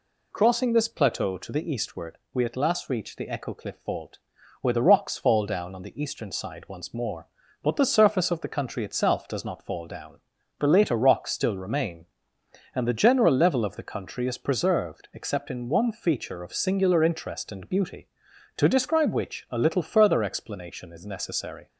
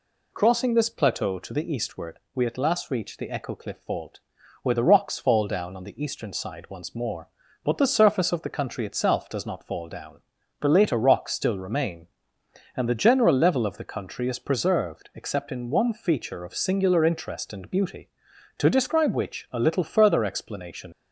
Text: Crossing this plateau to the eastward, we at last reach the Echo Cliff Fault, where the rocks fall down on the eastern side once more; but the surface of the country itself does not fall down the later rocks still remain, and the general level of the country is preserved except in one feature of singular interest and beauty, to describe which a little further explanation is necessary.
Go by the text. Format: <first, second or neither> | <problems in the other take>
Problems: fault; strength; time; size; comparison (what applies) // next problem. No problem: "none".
first | pauses between "down" and "the"; at 10.2 s; 0.38 s long; also in the first // stops before "is necessary"; at 20.9 s